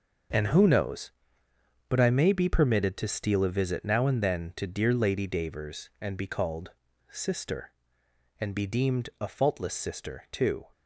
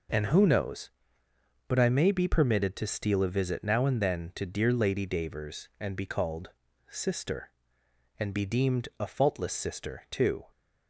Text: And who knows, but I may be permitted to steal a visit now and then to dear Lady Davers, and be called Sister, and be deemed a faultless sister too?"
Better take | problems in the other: second | gets quieter; strong; throughout; 9.5 dB // pauses between "called" and "Sister"; at 6.7 s; 0.38 s long; also in the second

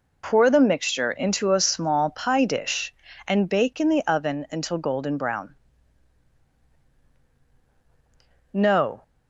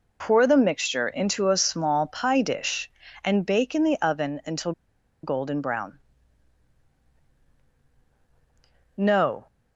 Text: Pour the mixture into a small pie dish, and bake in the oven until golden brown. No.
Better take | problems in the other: first | pauses between "until" and "golden"; noticeable; at 4.7 s; 0.52 s long

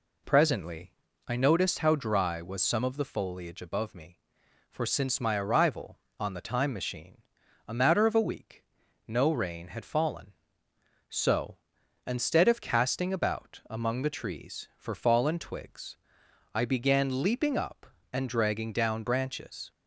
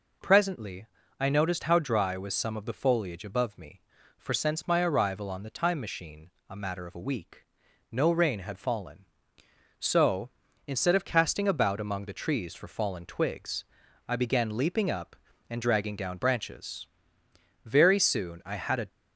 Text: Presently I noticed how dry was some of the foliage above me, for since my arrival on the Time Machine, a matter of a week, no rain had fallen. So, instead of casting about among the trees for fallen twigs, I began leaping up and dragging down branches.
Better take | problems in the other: first | pauses between "Presently" and "I"; slight; at 0.8 s; 0.34 s long; slight in the first // goes on to say "Very soon I had a"; noticeable; from 17.6 s on; 1.2 s long

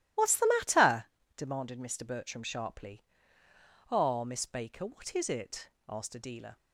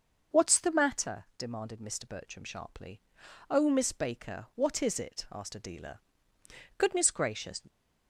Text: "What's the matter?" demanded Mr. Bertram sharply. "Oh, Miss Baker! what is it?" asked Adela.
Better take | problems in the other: first | starts louder than the rest; until 1.4 s; 6 dB // goes on to say "Goodness gracious"; noticeable; from 6.7 s on; 0.82 s long

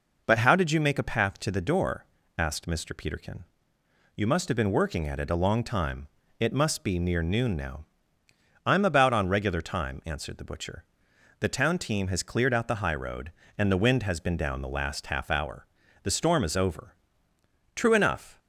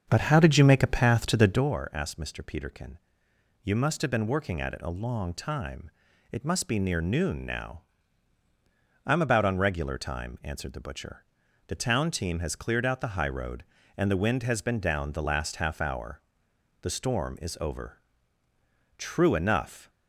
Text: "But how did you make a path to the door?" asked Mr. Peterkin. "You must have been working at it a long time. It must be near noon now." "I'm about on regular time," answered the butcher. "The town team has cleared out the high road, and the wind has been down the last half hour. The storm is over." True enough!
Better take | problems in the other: first | starts louder than the rest; until 1.7 s; 7 dB

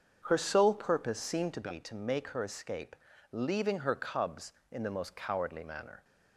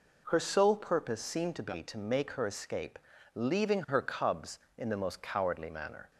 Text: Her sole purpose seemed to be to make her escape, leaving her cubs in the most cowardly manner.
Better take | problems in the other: second | starts louder than the rest; until 1.7 s; 6.5 dB

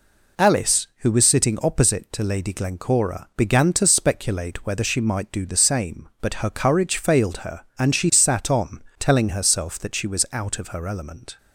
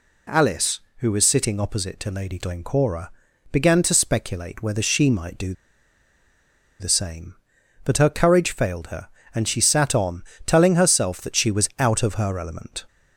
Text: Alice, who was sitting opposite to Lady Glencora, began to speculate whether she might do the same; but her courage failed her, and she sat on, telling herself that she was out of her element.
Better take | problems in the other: first | pauses between "do" and "the"; strong; at 5.5 s; 1.2 s long

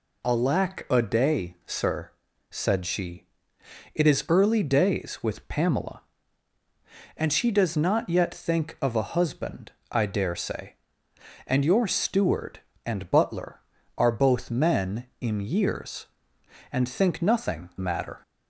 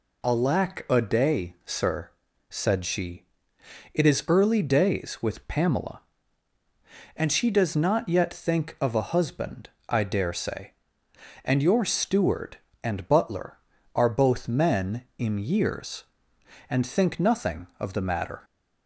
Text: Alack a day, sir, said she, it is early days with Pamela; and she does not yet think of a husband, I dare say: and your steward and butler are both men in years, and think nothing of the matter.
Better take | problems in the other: second | skips "of the"; at 17.7 s

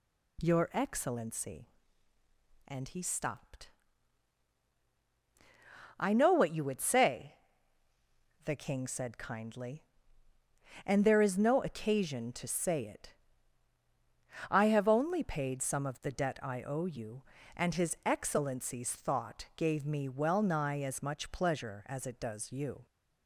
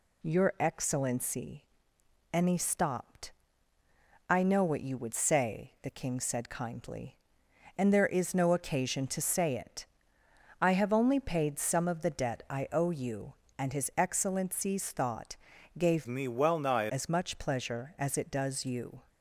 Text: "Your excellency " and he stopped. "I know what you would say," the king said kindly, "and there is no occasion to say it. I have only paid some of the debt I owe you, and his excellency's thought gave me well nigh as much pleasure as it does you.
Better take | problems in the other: first | pauses between "thought" and "gave"; at 15.3 s; 0.40 s long // changes voice from "me" to "nigh"; from 16.0 to 16.8 s; 0.8 s long

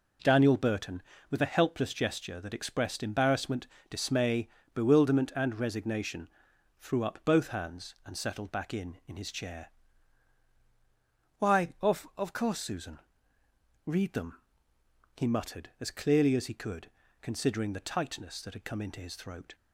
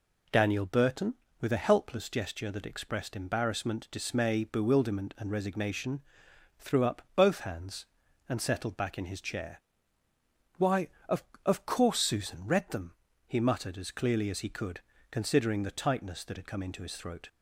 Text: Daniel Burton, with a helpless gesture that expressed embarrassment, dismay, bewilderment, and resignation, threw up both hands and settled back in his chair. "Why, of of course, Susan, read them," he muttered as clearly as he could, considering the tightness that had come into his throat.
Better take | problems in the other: second | says "in" twice; at 9.0 s

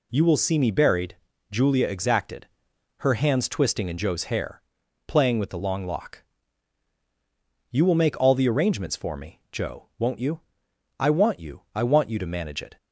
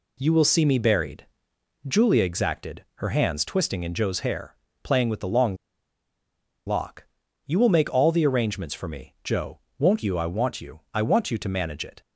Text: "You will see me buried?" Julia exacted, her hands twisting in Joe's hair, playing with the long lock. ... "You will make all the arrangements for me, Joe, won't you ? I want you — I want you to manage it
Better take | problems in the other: first | pauses between "long" and "lock"; at 5.5 s; 1.1 s long

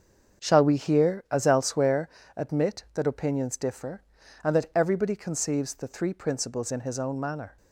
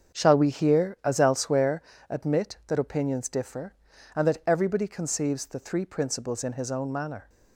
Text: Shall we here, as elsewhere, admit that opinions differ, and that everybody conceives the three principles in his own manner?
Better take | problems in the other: neither | starts louder than the rest; the same in both

